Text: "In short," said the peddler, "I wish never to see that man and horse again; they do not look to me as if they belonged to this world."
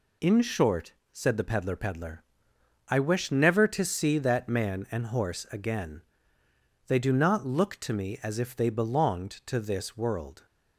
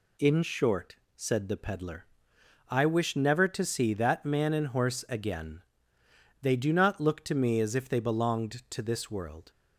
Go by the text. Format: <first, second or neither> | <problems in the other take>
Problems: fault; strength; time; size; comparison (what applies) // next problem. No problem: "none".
second | says "peddler" twice; at 1.7 s